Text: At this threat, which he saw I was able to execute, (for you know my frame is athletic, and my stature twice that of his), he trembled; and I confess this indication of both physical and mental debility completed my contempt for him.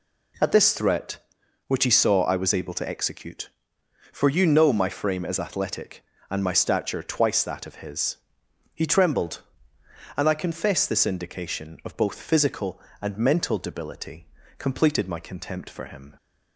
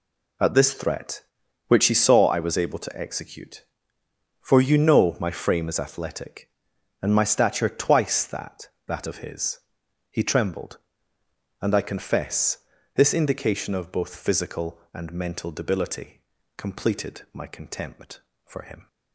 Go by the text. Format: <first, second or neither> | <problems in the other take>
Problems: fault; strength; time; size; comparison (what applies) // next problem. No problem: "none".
first | says "that" twice; at 8.8 s // pauses between "confess" and "this"; at 12.5 s; 0.38 s long // pauses between "debility" and "completed"; slight; at 16.2 s; 0.36 s long; slight in the first